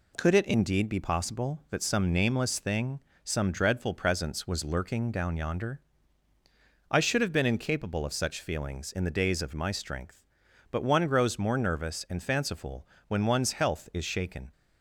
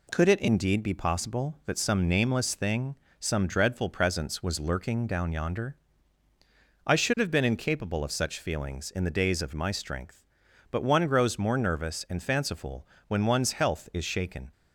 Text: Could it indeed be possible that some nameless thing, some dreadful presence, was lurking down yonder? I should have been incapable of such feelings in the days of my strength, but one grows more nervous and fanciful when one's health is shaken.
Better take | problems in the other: neither | pauses between "fanciful" and "when"; slight; the same in both

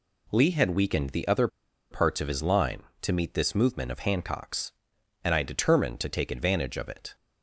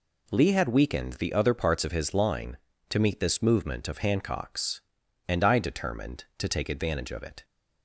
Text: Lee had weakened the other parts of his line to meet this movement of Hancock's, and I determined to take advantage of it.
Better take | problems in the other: second | pauses between "other" and "parts"; at 1.4 s; 0.42 s long

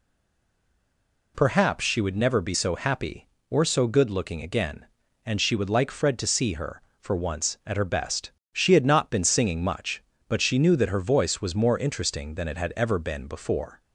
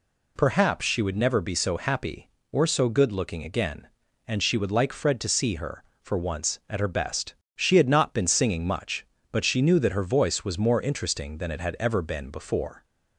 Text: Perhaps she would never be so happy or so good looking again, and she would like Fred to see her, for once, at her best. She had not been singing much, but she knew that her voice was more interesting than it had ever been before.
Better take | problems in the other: second | stays silent before the first word; noticeable; until 1.3 s; 1.3 s long

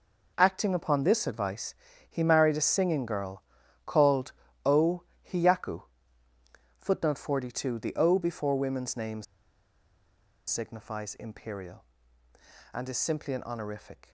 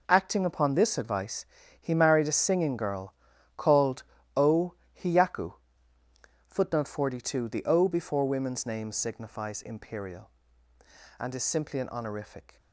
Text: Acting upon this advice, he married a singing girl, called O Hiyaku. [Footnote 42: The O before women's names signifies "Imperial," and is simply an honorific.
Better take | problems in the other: second | pauses between "called" and "O"; slight; at 4.3 s; 0.34 s long; slight in the second // pauses between "O" and "Hiyaku"; slight; at 5.0 s; 0.28 s long; slight in the second // pauses between "names" and "signifies"; strong; at 9.2 s; 1.2 s long

